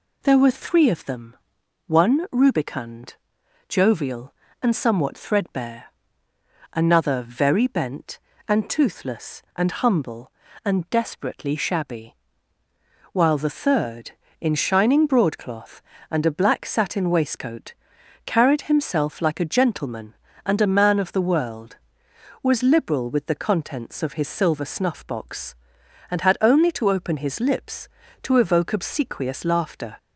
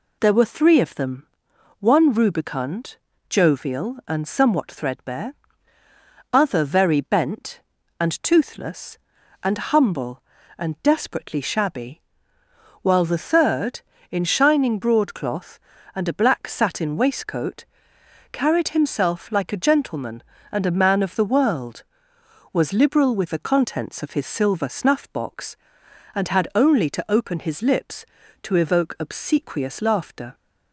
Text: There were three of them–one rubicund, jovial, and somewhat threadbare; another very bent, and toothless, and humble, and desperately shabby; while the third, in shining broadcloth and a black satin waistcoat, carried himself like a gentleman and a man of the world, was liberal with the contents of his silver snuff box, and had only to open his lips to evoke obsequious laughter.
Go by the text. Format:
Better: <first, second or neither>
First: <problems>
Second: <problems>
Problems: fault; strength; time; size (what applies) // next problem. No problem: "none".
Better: first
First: none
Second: says "other" for "another"; at 6.3 s